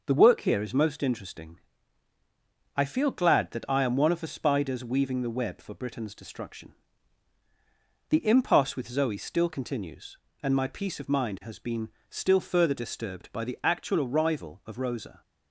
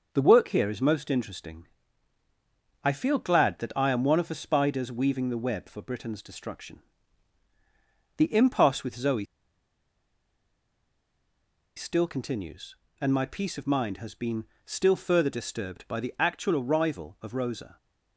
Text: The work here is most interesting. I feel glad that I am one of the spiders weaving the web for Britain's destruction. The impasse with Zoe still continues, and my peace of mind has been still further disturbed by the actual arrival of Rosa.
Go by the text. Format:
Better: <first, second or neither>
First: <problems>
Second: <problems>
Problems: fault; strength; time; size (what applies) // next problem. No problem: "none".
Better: first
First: pauses between "been" and "still"; slight; at 11.8 s; 0.18 s long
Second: pauses between "Zoe" and "still"; strong; at 9.2 s; 2.5 s long // pauses between "been" and "still"; slight; at 14.4 s; 0.18 s long